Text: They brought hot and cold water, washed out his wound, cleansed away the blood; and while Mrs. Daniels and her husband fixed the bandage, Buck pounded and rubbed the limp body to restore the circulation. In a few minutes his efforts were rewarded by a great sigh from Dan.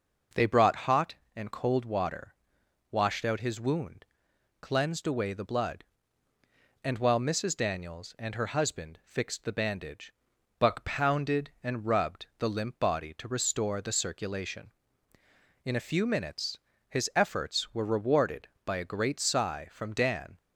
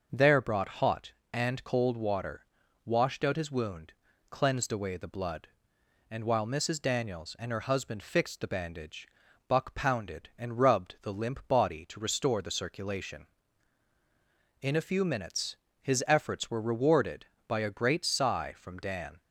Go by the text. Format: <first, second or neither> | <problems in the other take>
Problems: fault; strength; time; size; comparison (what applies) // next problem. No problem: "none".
first | starts louder than the rest; noticeable; until 1.1 s; 6 dB // says "There" for "They"; at 0.1 s // pauses between "minutes" and "his"; slight; at 15.5 s; 0.22 s long; slight in the first